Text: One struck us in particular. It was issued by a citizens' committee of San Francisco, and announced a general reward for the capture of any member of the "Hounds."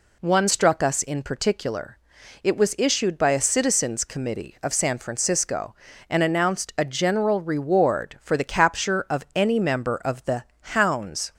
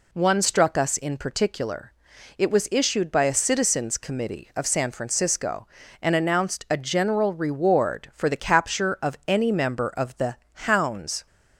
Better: neither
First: pauses between "the" and "Hounds"; slight; at 10.4 s; 0.30 s long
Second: pauses between "the" and "Hounds"; slight; at 10.3 s; 0.30 s long

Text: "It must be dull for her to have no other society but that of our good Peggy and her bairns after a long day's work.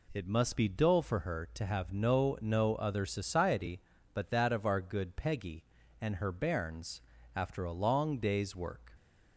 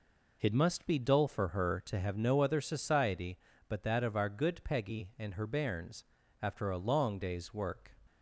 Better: second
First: says "no" twice; at 2.3 s // pauses between "bairns" and "after"; slight; at 7.0 s; 0.34 s long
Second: pauses between "bairns" and "after"; slight; at 6.0 s; 0.36 s long

